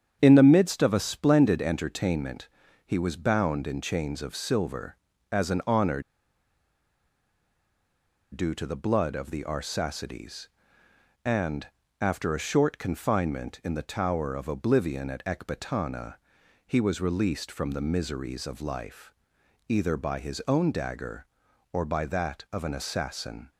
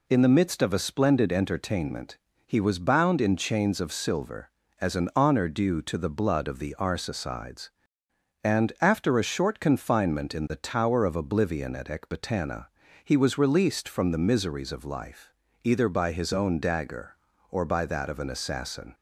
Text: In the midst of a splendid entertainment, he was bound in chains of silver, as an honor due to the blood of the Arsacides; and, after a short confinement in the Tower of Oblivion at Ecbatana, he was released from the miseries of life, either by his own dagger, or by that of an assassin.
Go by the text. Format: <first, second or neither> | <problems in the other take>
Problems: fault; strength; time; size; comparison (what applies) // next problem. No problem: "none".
second | starts louder than the rest; strong; until 1.2 s; 8.5 dB // pauses between "honor" and "due"; strong; at 6.0 s; 2.3 s long